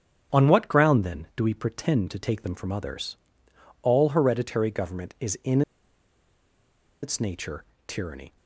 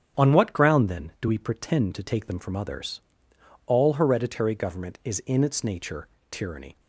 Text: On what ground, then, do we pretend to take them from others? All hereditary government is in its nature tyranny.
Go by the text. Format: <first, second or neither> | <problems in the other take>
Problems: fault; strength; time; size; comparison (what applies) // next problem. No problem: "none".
second | starts louder than the rest; strong; until 1.4 s; 8 dB; strong in the second // pauses between "in" and "its"; strong; at 5.6 s; 1.4 s long // pauses between "nature" and "tyranny"; slight; at 7.6 s; 0.24 s long; slight in the second